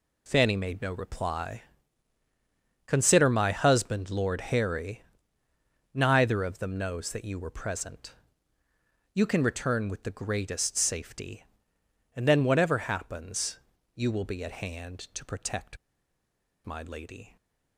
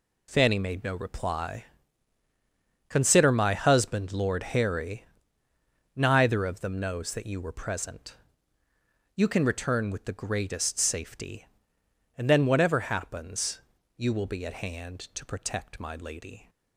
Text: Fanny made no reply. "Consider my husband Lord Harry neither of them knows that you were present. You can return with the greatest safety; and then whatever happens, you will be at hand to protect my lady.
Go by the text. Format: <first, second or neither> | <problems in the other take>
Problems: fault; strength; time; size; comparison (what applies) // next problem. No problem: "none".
second | pauses between "Harry" and "neither"; noticeable; at 5.0 s; 0.90 s long; noticeable in the second // pauses between "protect" and "my"; noticeable; at 15.7 s; 0.88 s long